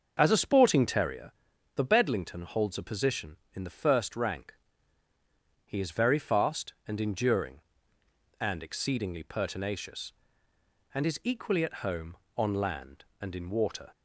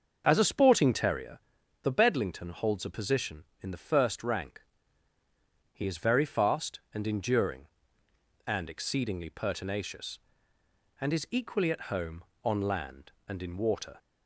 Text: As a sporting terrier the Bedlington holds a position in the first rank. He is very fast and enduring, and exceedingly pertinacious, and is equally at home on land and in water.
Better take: neither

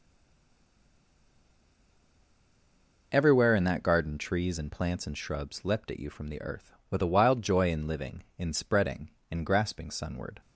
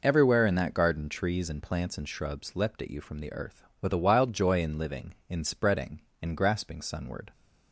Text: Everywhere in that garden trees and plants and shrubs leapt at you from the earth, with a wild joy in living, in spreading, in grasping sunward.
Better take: second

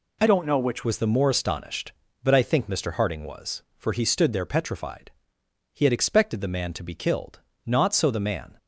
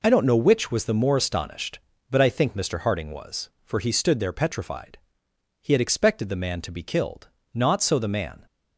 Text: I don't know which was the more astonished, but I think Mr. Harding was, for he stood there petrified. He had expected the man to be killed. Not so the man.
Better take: second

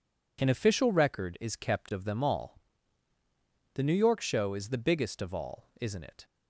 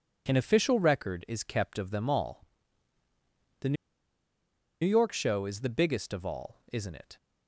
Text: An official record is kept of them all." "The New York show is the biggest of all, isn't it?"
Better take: first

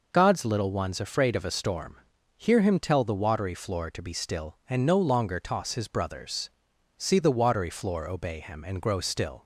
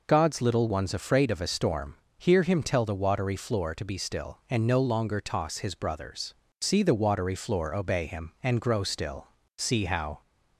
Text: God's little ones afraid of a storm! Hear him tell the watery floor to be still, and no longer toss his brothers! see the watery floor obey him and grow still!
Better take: first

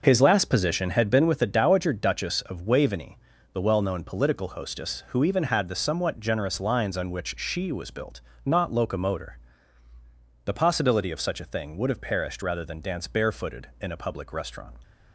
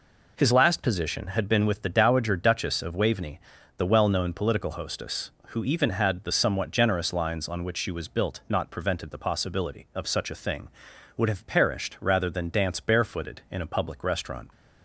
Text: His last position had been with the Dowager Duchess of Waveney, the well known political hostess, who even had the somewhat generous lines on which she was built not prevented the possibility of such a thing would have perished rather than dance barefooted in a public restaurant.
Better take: second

